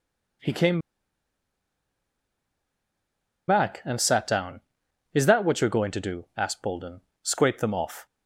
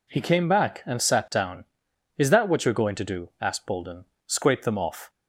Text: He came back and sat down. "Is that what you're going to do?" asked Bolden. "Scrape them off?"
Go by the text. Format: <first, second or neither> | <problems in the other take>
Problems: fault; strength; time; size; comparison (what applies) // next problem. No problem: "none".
second | pauses between "came" and "back"; strong; at 0.8 s; 2.6 s long